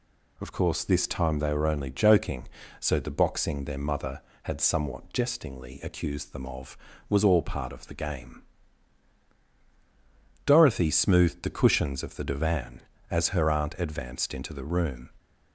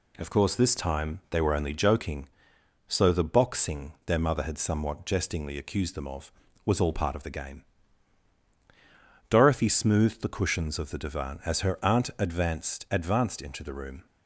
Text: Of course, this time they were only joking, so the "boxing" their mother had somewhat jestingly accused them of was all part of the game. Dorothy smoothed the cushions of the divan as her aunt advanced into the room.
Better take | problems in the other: first | says "advanced" twice; at 12.8 s

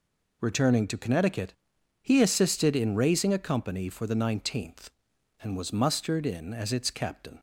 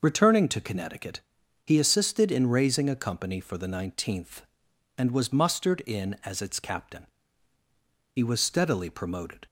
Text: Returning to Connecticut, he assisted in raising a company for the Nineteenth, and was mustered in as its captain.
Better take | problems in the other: first | goes on to say "He was steadily promoted"; noticeable; from 8.1 s on; 1.3 s long

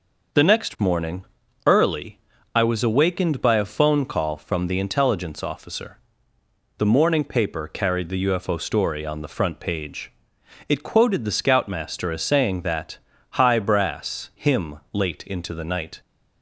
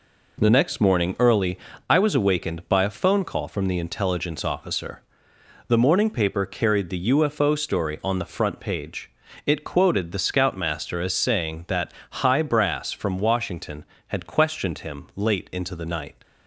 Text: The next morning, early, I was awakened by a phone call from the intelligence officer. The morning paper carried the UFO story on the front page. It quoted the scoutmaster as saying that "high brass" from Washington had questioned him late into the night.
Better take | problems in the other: second | pauses between "that" and "high"; at 12.9 s; 0.40 s long; slight in the second // skips "from Washington had questioned"; at 14.3 s

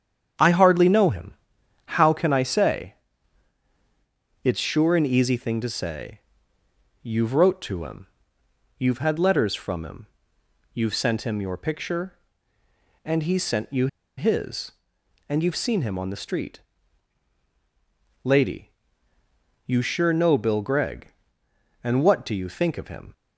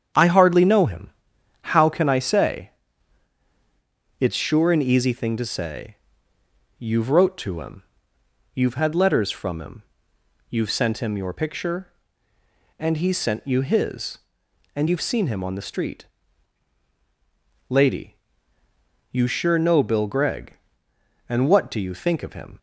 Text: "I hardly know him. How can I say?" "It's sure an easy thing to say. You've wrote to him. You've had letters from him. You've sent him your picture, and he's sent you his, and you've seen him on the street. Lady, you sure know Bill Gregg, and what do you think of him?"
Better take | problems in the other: second | starts louder than the rest; strong; until 2.0 s; 9 dB; strong in the second // pauses between "you" and "his"; slight; at 13.8 s; 0.30 s long

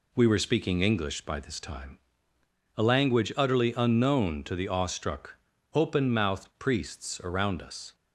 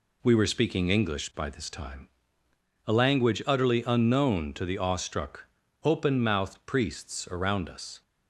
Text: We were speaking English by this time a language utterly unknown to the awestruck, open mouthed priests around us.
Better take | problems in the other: neither | pauses between "time" and "a"; noticeable; the same in both

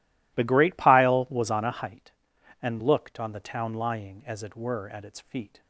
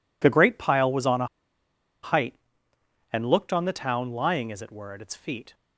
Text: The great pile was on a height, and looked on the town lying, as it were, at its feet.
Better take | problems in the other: first | pauses between "a" and "height"; noticeable; at 1.2 s; 0.76 s long

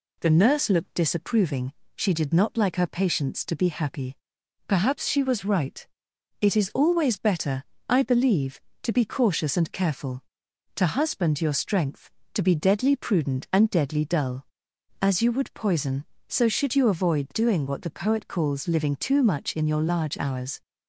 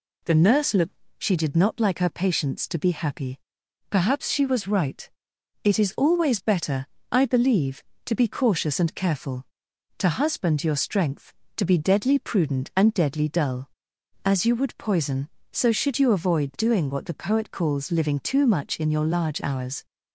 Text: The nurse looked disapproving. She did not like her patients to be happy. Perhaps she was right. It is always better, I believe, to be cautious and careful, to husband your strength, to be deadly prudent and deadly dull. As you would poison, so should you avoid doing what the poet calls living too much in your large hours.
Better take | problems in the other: first | skips "disapproving"; at 1.0 s

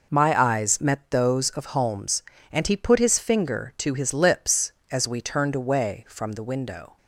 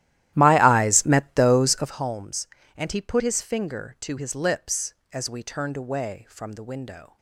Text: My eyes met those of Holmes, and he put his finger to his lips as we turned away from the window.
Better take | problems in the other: first | starts louder than the rest; strong; until 2.0 s; 14 dB

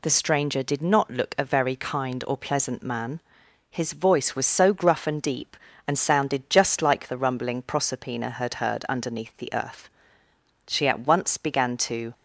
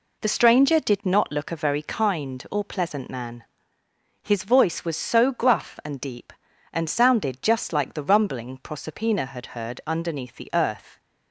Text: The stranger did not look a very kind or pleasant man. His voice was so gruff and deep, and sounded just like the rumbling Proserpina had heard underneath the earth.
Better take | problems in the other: second | goes on to say "She at once began to"; from 10.6 s on; 1.4 s long

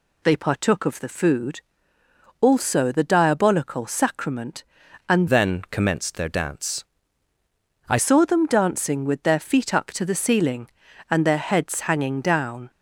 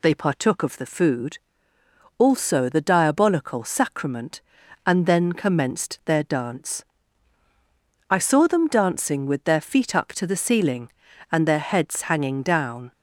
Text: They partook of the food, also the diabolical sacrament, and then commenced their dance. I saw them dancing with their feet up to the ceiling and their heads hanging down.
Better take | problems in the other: second | changes voice from "then" to "I"; from 5.2 to 7.9 s; 2.7 s long

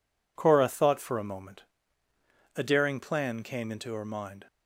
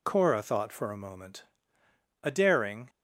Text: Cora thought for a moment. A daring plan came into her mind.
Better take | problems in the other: first | stops before "plan came into her mind"; at 2.8 s

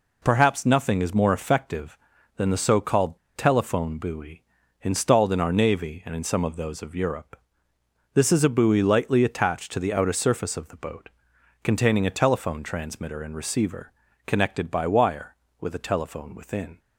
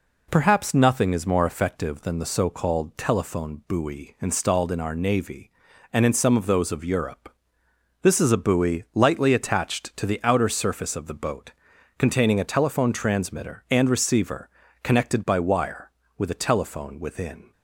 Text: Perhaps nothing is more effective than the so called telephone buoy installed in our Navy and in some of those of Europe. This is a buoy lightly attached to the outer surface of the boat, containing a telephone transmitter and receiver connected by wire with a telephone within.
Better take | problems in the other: second | pauses between "called" and "telephone"; slight; at 3.1 s; 0.18 s long // pauses between "buoy" and "installed"; at 4.4 s; 0.38 s long // pauses between "receiver" and "connected"; slight; at 13.9 s; 0.36 s long; slight in the second

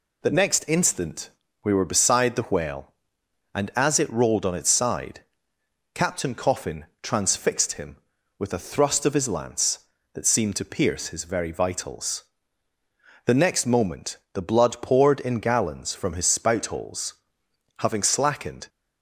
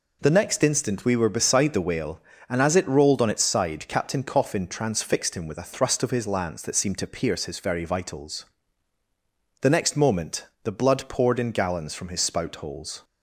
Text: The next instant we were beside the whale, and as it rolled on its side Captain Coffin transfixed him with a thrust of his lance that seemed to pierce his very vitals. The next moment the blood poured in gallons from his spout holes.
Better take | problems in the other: second | pauses between "instant" and "we"; slight; at 1.2 s; 0.34 s long // pauses between "side" and "Captain"; noticeable; at 5.2 s; 0.72 s long // pauses between "Coffin" and "transfixed"; slight; at 6.8 s; 0.16 s long // pauses between "moment" and "the"; slight; at 14.1 s; 0.16 s long; slight in the second // goes on to say "Having slackened"; noticeable; from 17.8 s on; 0.88 s long

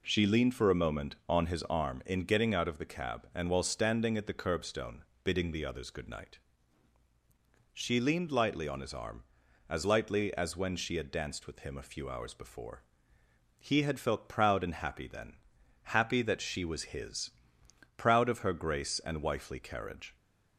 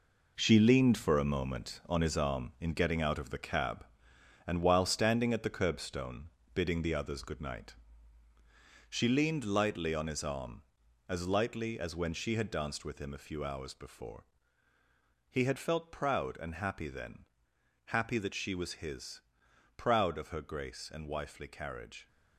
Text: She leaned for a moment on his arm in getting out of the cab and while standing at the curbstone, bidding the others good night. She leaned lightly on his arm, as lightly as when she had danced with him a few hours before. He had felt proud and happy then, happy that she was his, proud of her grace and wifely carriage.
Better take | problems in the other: first | gets quieter; strong; throughout; 8.5 dB

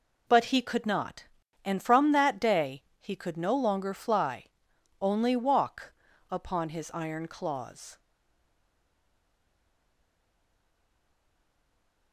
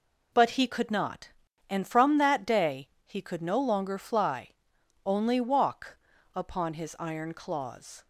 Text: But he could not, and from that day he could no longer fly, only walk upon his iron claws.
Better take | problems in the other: second | pauses between "day" and "he"; slight; at 2.8 s; 0.16 s long; slight in the second // pauses between "walk" and "upon"; slight; at 5.9 s; 0.36 s long; slight in the second // stays silent after the last word; strong; from 7.9 s on; 4.2 s long

